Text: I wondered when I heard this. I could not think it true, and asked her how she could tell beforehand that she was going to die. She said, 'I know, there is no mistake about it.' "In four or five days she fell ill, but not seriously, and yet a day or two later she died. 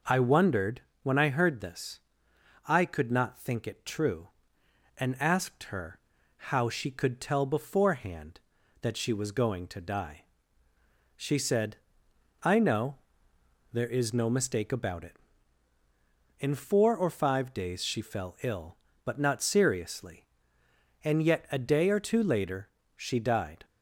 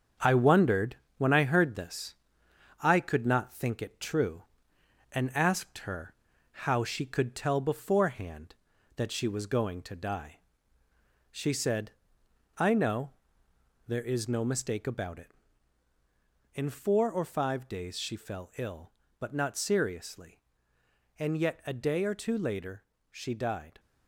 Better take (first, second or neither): first